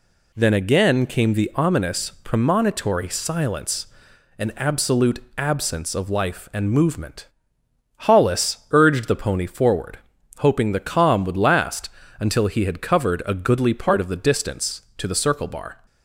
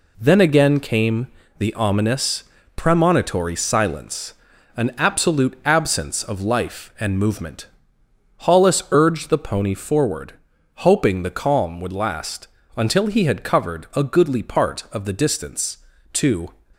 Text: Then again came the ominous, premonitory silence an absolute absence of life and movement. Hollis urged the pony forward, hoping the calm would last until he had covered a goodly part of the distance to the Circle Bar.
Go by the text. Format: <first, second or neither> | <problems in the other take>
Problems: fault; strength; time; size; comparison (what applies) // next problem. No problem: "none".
first | pauses between "came" and "the"; slight; at 1.2 s; 0.30 s long // pauses between "silence" and "an"; at 4.3 s; 0.44 s long; noticeable in the first // pauses between "last" and "until"; slight; at 12.4 s; 0.28 s long; slight in the first // stops before "the Circle Bar"; at 16.7 s